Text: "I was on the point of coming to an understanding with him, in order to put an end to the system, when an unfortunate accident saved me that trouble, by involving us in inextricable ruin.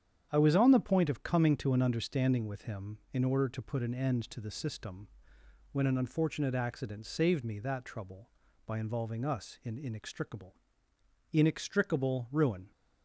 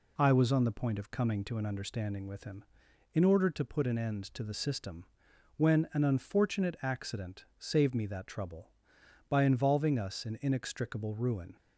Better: second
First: starts louder than the rest; strong; until 1.3 s; 8.5 dB // says "inextricable" twice; at 11.3 s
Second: none

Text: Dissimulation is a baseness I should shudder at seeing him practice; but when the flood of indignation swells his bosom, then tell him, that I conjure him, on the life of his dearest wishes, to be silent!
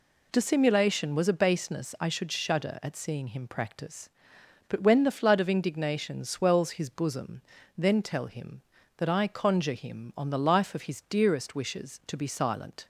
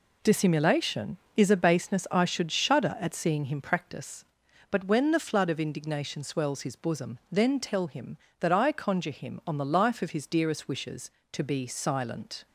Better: second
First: says "was" for "is"; at 1.1 s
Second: none

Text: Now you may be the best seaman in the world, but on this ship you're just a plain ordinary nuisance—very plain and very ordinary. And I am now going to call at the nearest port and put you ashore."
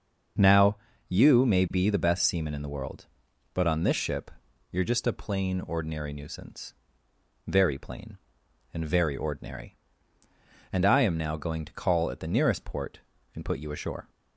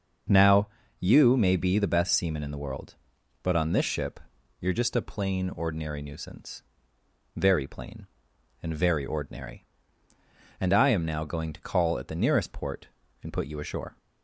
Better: neither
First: starts louder than the rest; until 1.7 s; 6.5 dB // pauses between "Now" and "you"; slight; at 0.7 s; 0.32 s long // pauses between "ship" and "you're"; at 4.3 s; 0.40 s long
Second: starts louder than the rest; until 1.6 s; 6.5 dB // pauses between "Now" and "you"; slight; at 0.6 s; 0.32 s long // pauses between "ship" and "you're"; at 4.2 s; 0.40 s long

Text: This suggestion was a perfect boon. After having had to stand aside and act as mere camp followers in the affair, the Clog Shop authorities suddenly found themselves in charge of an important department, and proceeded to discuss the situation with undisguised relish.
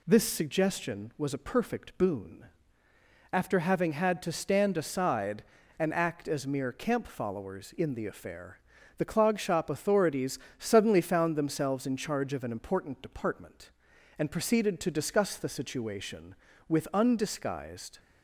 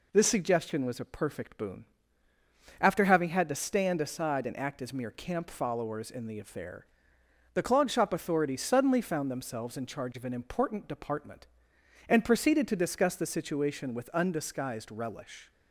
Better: second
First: pauses between "authorities" and "suddenly"; slight; at 10.3 s; 0.22 s long // stops before "relish"; at 17.9 s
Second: none

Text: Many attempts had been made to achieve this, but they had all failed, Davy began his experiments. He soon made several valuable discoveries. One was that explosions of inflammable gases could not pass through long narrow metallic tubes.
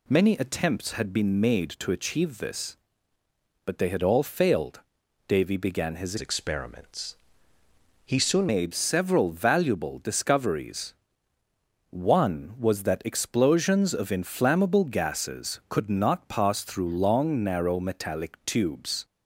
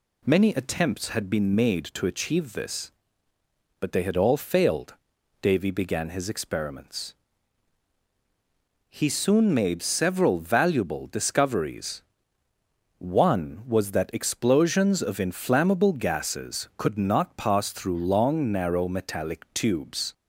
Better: second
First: changes voice from "experiments" to "soon"; from 6.1 to 8.4 s; 2.3 s long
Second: none

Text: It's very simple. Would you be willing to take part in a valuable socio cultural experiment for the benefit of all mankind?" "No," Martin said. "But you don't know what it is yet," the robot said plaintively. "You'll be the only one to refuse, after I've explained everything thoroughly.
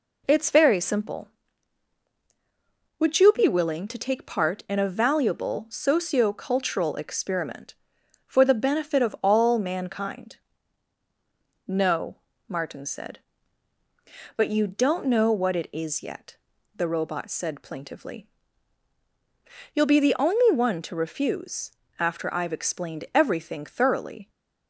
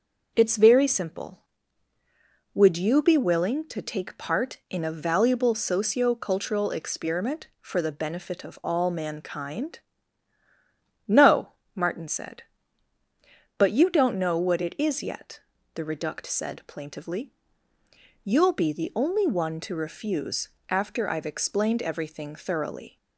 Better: first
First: none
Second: starts louder than the rest; noticeable; until 1.3 s; 6 dB // says "reduct" for "robot"; at 15.8 s

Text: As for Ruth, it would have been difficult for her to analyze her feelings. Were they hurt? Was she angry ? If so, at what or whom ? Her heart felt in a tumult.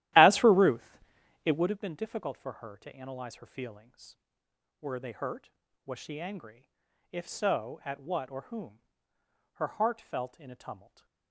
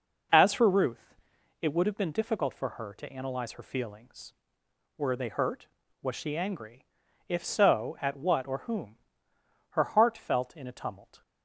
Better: second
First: starts louder than the rest; strong; until 1.8 s; 14 dB // stays silent after the last word; slight; from 10.7 s on; 0.6 s long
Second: none

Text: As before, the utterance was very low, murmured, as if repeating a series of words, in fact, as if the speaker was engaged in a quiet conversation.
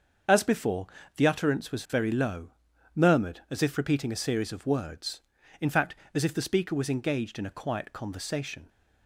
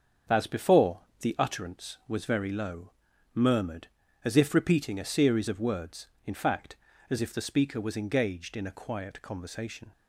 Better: neither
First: starts louder than the rest; until 1.5 s; 6.5 dB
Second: starts louder than the rest; strong; until 1.5 s; 7.5 dB

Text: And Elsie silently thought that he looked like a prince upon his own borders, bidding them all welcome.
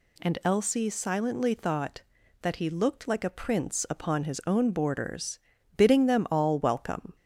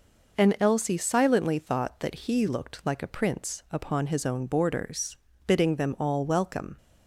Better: neither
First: none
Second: none

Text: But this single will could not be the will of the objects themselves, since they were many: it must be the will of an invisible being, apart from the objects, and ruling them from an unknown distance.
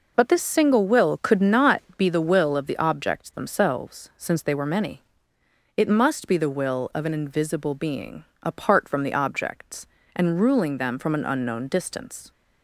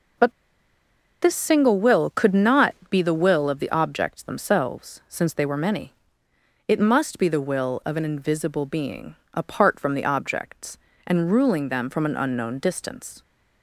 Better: first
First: pauses between "not" and "be"; slight; at 1.8 s; 0.16 s long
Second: pauses between "But" and "this"; noticeable; at 0.3 s; 0.89 s long // pauses between "not" and "be"; slight; at 2.7 s; 0.16 s long

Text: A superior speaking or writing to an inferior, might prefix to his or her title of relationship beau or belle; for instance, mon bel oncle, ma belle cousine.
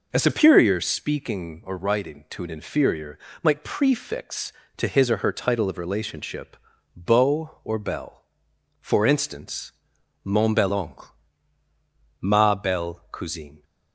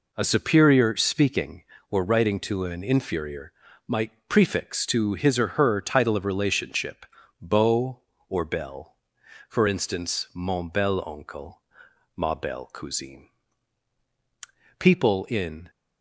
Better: first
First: pauses between "relationship" and "beau"; at 6.5 s; 0.40 s long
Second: pauses between "relationship" and "beau"; slight; at 7.0 s; 0.36 s long // goes on to say "People in"; noticeable; from 14.7 s on; 0.90 s long

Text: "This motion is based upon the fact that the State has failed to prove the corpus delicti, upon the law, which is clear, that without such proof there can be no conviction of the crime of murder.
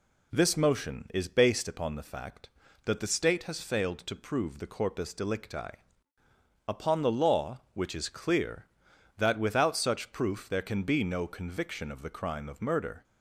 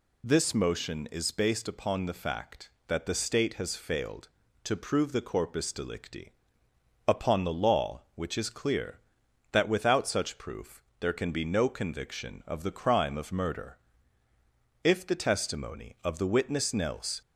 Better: first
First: none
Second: pauses between "proof" and "there"; slight; at 10.8 s; 0.16 s long // goes on to say "If the testimony of the witness Nels"; strong; from 14.8 s on; 2.3 s long

